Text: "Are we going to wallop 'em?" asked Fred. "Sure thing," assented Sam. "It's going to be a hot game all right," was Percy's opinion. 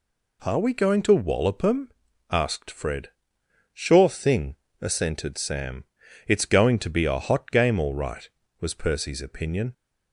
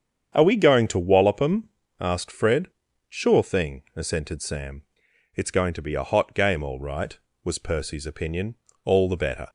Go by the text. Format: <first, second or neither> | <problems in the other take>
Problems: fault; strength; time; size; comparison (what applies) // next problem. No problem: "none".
first | starts louder than the rest; strong; until 1.3 s; 8 dB // goes on to say "All the better"; noticeable; from 8.8 s on; 0.64 s long